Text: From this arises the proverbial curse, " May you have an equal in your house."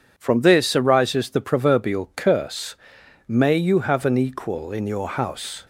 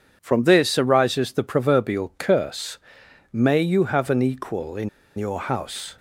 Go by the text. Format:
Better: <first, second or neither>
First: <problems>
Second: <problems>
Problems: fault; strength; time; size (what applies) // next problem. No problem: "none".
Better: first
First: starts louder than the rest; until 1.1 s; 7 dB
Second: starts louder than the rest; until 1.2 s; 6.5 dB // pauses between "in" and "your"; slight; at 4.8 s; 0.29 s long